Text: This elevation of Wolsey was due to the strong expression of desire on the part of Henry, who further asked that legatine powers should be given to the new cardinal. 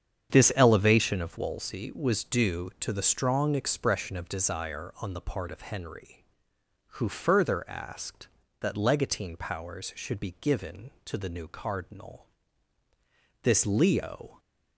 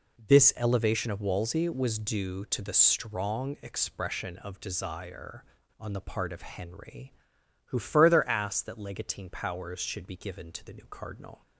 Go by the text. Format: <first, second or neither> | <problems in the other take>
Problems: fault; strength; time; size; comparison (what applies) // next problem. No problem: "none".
second | starts louder than the rest; strong; until 1.3 s; 8 dB // goes on to say "This Leo"; noticeable; from 13.4 s on; 0.98 s long